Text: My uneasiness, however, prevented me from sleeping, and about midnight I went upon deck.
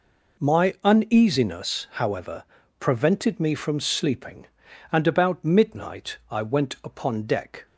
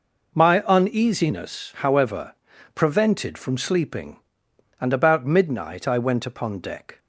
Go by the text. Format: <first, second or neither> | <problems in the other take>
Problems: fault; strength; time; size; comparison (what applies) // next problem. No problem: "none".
first | skips "me"; at 3.3 s